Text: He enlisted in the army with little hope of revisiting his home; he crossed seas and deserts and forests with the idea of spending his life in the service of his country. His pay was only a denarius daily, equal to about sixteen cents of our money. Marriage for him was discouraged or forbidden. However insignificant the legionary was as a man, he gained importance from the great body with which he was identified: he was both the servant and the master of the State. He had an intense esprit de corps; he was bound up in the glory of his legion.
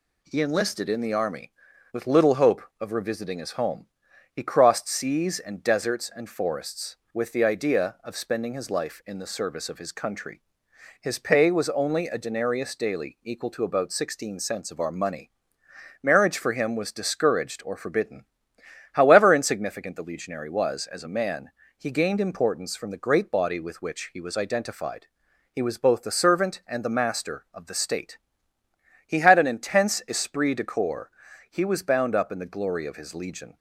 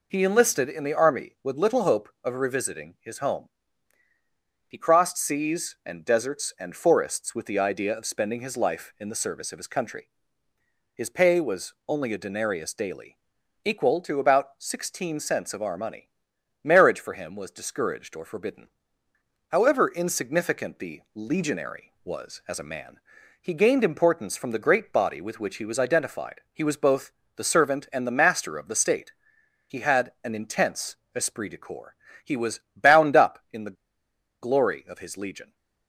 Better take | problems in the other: first | pauses between "both" and "the"; slight; at 27.1 s; 0.24 s long // pauses between "intense" and "esprit"; slight; at 30.9 s; 0.18 s long // pauses between "was" and "bound"; slight; at 32.5 s; 0.16 s long // pauses between "the" and "glory"; noticeable; at 33.7 s; 0.67 s long

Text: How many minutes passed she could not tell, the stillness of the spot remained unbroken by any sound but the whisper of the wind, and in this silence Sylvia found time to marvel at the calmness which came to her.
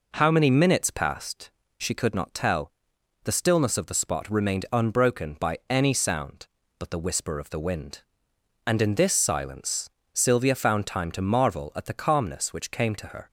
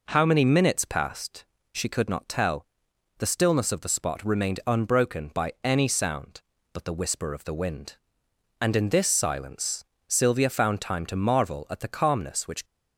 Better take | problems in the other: first | pauses between "passed" and "she"; slight; at 1.4 s; 0.28 s long; slight in the first // pauses between "silence" and "Sylvia"; slight; at 9.8 s; 0.24 s long; slight in the first // stops before "came to her"; at 12.6 s

